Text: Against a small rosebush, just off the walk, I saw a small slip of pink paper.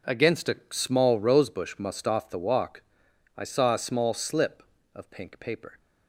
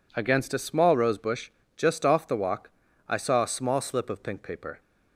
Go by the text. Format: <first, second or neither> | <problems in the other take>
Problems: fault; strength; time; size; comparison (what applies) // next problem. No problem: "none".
second | says "must" for "just"; at 1.7 s